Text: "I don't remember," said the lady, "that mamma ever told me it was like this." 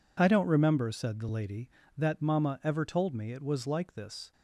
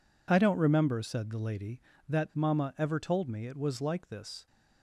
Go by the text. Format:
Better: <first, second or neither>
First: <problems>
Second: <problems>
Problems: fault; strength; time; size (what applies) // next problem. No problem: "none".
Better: neither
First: none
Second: none